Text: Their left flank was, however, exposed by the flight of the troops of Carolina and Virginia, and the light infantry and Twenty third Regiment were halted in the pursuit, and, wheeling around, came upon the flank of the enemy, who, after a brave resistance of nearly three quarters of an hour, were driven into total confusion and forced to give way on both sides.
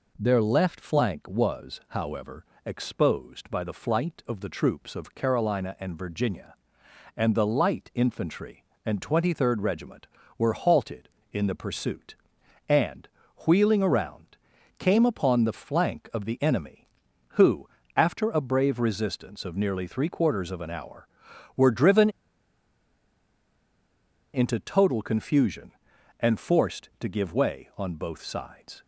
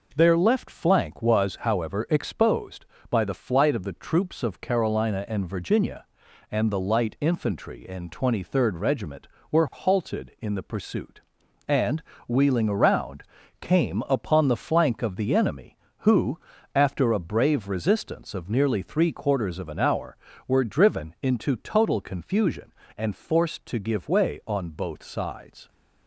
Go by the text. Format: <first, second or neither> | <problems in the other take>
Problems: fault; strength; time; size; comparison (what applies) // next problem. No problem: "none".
second | pauses between "driven" and "into"; strong; at 22.0 s; 2.2 s long